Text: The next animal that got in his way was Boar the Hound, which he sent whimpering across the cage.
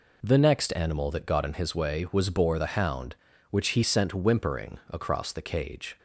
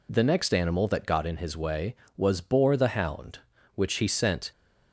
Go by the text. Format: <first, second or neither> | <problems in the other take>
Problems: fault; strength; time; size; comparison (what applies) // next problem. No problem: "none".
first | stops before "whimpering across the cage"; at 4.5 s